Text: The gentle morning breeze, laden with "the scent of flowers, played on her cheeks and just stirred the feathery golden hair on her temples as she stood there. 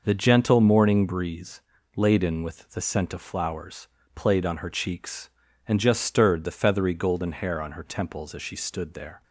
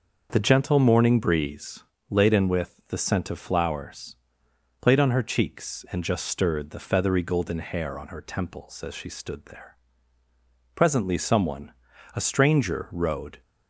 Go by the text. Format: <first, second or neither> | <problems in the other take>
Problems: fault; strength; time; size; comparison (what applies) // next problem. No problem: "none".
first | starts louder than the rest; until 1.3 s; 6 dB // goes on to say "Presently someone a stranger rode"; strong; from 10.7 s on; 2.6 s long